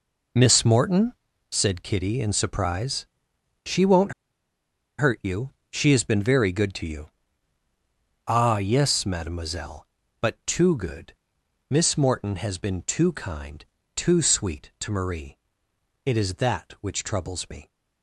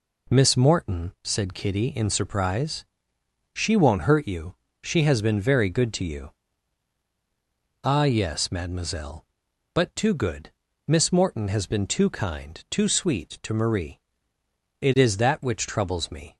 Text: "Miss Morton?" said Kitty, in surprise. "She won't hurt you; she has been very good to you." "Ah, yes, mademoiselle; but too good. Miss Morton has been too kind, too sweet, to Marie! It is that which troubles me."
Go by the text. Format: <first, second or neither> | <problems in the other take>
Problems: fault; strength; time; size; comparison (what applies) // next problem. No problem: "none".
second | pauses between "won't" and "hurt"; noticeable; at 4.1 s; 0.88 s long